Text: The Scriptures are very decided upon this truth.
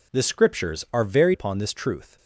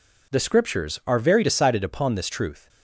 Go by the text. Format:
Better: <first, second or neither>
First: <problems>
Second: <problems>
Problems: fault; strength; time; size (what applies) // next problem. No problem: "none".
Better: second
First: skips "decided"; at 1.3 s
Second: none